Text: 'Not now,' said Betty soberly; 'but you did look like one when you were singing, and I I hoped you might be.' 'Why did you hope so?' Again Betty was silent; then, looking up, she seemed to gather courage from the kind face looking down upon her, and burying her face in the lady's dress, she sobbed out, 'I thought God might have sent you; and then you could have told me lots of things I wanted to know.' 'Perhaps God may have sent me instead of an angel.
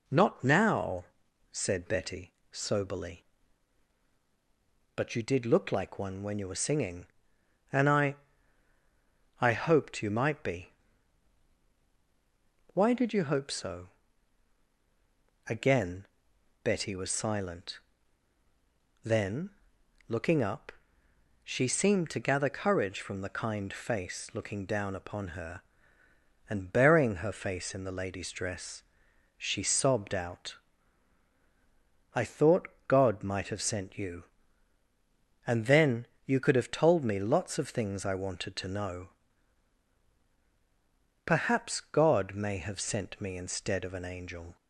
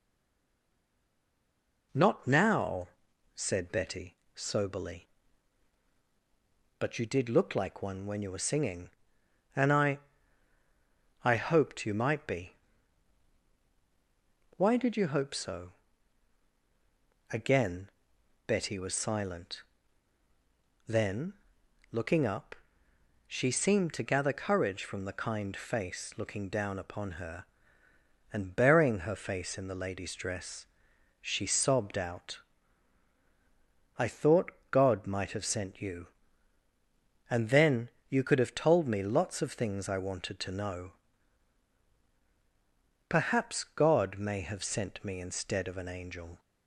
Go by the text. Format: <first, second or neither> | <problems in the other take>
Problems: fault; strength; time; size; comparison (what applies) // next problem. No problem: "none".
first | stays silent before the first word; noticeable; until 1.9 s; 1.9 s long // pauses between "Betty" and "soberly"; slight; at 4.1 s; 0.20 s long; slight in the first // pauses between "I" and "I"; at 9.9 s; 1.2 s long; also in the first // pauses between "Again" and "Betty"; noticeable; at 17.8 s; 0.56 s long; noticeable in the first // pauses between "then" and "you"; slight; at 37.8 s; 0.20 s long; slight in the first